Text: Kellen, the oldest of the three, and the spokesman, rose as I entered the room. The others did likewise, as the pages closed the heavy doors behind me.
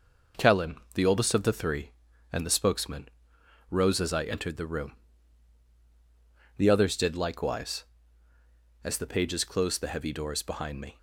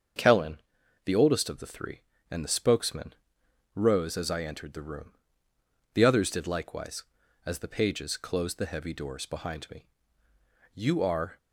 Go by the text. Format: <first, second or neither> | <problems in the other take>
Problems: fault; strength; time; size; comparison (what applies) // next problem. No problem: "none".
first | starts louder than the rest; until 1.6 s; 7 dB // goes on to say "You are"; noticeable; from 10.7 s on; 0.64 s long